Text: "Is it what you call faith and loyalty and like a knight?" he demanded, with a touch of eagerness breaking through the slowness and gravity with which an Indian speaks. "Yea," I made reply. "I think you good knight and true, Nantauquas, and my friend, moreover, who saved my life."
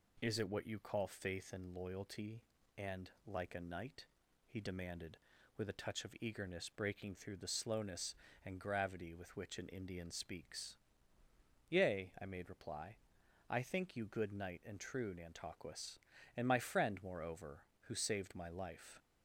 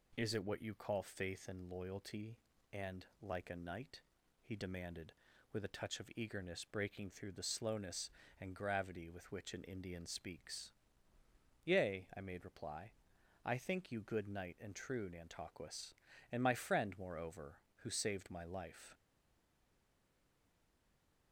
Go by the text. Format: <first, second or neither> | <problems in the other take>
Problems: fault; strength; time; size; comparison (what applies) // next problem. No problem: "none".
first | pauses between "and" and "like"; slight; at 3.0 s; 0.16 s long; slight in the first // stays silent after the last word; from 18.9 s on; 2.4 s long